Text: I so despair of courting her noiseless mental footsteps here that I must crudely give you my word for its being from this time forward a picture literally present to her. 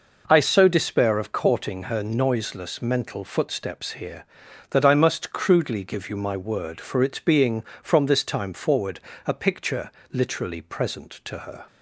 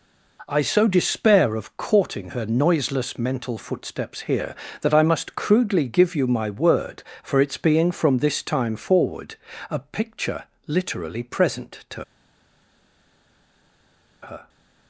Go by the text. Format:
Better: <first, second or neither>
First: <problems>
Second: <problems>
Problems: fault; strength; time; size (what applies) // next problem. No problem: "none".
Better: first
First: pauses between "forward" and "a"; slight; at 9.0 s; 0.26 s long // pauses between "picture" and "literally"; slight; at 9.9 s; 0.22 s long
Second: pauses between "forward" and "a"; slight; at 9.3 s; 0.34 s long // pauses between "picture" and "literally"; slight; at 10.4 s; 0.22 s long // pauses between "to" and "her"; strong; at 12.0 s; 2.1 s long